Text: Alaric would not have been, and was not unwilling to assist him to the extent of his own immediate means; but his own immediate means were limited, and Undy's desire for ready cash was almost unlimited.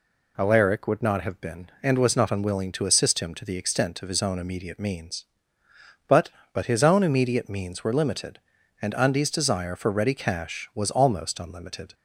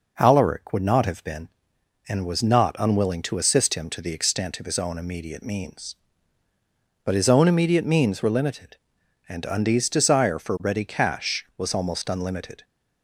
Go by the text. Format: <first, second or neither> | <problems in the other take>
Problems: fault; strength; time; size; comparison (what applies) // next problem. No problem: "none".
second | says "but" twice; at 6.5 s